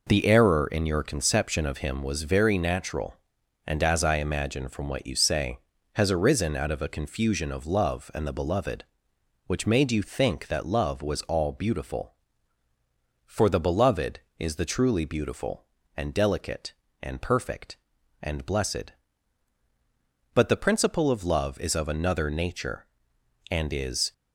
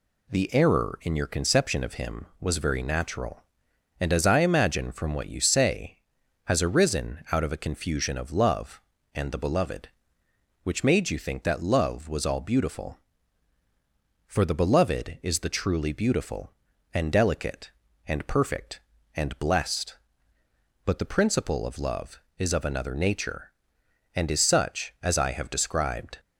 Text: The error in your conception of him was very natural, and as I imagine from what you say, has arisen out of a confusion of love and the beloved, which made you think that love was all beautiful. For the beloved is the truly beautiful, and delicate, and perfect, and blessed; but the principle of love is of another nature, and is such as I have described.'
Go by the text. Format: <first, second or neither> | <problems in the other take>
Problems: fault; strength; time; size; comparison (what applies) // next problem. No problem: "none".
second | stops before "such as I have described"; at 24.1 s